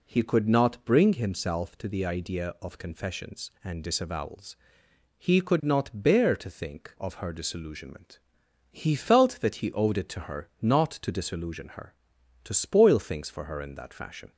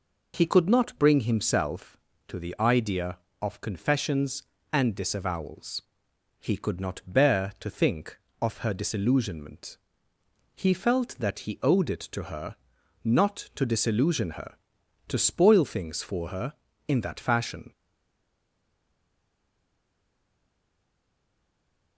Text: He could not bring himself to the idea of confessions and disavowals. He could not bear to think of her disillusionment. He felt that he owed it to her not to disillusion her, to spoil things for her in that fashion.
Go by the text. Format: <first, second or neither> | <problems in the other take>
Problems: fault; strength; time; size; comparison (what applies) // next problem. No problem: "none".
first | pauses between "her" and "not"; noticeable; at 12.5 s; 0.48 s long // stays silent after the last word; strong; from 17.7 s on; 4.2 s long